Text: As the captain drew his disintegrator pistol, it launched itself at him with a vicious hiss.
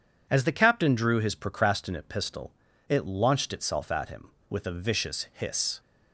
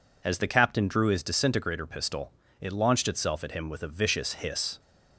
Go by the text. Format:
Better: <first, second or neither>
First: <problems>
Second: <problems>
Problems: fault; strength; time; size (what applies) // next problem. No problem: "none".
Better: second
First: says "procrastinate" for "disintegrator"; at 1.3 s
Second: none